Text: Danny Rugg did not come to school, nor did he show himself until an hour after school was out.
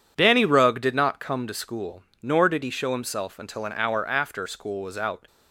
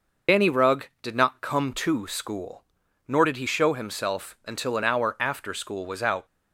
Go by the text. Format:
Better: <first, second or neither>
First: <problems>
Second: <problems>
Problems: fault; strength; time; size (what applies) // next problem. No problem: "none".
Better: first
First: none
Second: loses the start of "Danny"; at 0.2 s; 75 ms